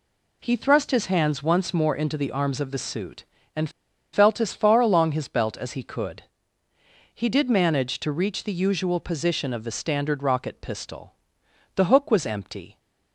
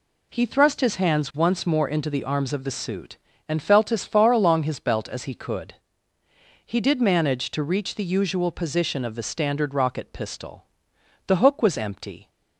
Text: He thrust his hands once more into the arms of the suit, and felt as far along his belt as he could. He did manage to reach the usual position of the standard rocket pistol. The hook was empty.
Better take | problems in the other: second | pauses between "and" and "felt"; at 3.6 s; 0.43 s long

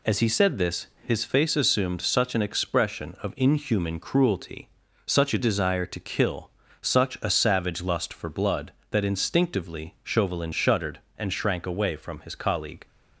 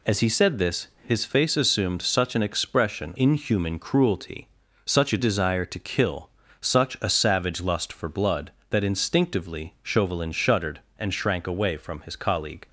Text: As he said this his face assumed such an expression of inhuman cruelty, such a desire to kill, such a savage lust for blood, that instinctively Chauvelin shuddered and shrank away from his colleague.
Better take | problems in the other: first | pauses between "this" and "his"; slight; at 0.8 s; 0.18 s long; slight in the first // skips "of"; at 3.1 s

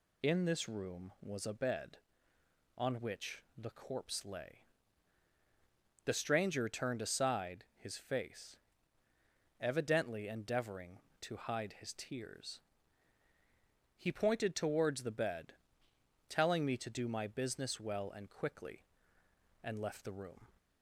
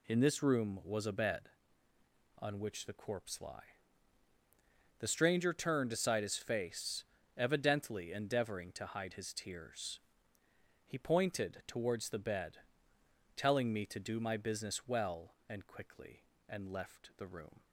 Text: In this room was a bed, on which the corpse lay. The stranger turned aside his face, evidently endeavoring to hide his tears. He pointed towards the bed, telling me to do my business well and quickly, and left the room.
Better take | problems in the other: first | says "lie" for "lay"; at 3.4 s

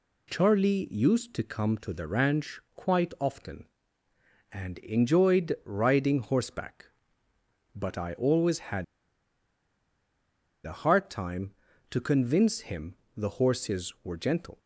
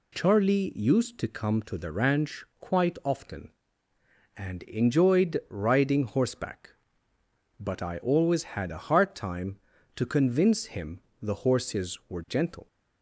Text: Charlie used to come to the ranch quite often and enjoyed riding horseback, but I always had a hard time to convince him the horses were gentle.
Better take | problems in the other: second | pauses between "had" and "a"; strong; at 8.8 s; 1.7 s long // pauses between "him" and "the"; slight; at 12.9 s; 0.20 s long; slight in the second

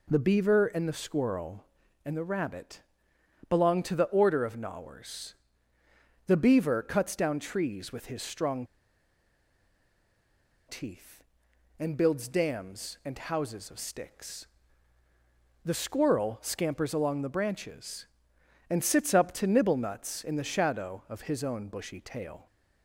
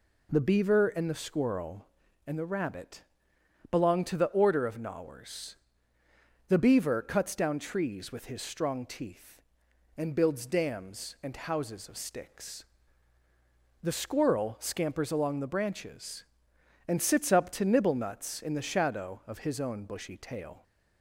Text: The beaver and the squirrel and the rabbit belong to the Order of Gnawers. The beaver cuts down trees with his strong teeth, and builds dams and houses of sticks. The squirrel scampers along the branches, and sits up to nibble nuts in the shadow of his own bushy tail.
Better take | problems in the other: second | pauses between "rabbit" and "belong"; noticeable; at 2.8 s; 0.70 s long; noticeable in the second // pauses between "strong" and "teeth"; strong; at 8.6 s; 2.0 s long

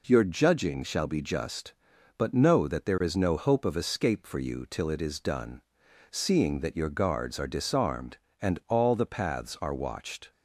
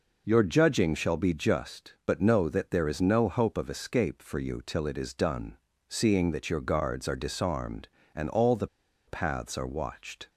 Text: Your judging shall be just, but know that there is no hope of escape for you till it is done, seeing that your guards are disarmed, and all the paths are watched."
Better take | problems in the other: first | pauses between "the" and "paths"; at 8.6 s; 0.41 s long

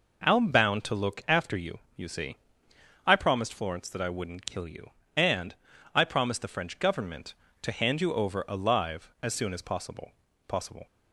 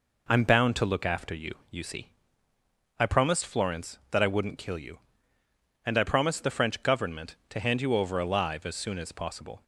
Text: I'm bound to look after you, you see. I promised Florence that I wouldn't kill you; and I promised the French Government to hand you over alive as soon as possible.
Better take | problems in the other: second | pauses between "and" and "I"; at 5.5 s; 0.40 s long // says "possible" twice; at 10.4 s

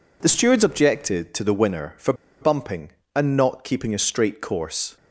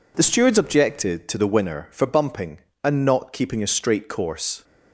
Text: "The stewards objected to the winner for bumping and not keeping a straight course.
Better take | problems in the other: second | pauses between "for" and "bumping"; slight; at 2.1 s; 0.27 s long

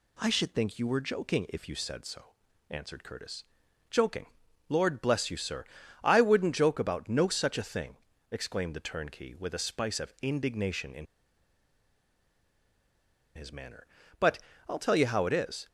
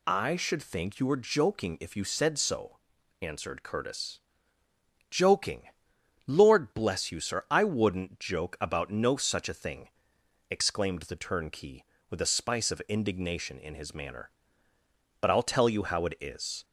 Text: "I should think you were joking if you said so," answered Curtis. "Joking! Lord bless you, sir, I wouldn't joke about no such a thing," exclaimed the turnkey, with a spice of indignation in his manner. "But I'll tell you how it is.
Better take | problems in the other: second | pauses between "in" and "his"; strong; at 11.0 s; 2.3 s long // pauses between "But" and "I'll"; slight; at 14.3 s; 0.26 s long

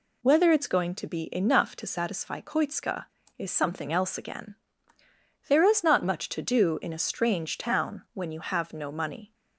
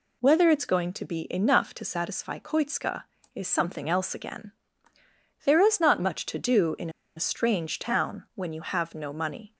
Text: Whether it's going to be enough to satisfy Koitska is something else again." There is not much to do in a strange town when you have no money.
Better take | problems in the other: first | pauses between "in" and "a"; slight; at 6.9 s; 0.26 s long

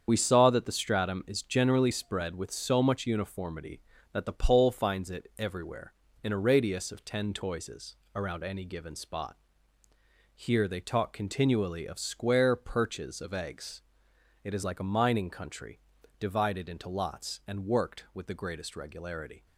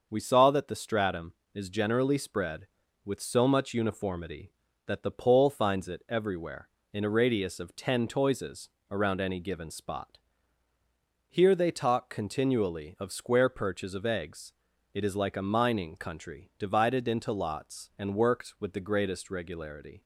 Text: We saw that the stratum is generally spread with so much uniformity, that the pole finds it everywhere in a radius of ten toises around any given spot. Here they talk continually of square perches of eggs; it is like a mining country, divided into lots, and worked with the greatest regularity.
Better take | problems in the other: second | loses the start of "We"; at 0.0 s; 45 ms // starts louder than the rest; strong; until 1.0 s; 7.5 dB; also in the second // pauses between "toises" and "around"; slight; at 7.9 s; 0.18 s long; slight in the second

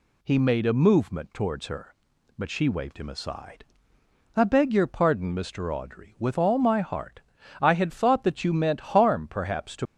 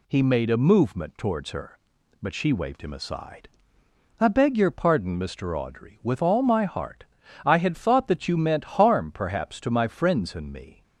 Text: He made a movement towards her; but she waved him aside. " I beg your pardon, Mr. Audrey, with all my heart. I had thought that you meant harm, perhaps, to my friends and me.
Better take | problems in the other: second | stops before "my friends and me"; at 9.8 s

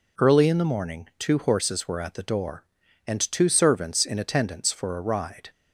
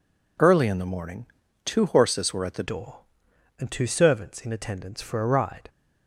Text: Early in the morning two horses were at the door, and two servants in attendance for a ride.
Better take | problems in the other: first | pauses between "morning" and "two"; at 1.2 s; 0.38 s long // changes voice at "door"; from 2.6 s on; 3.0 s long

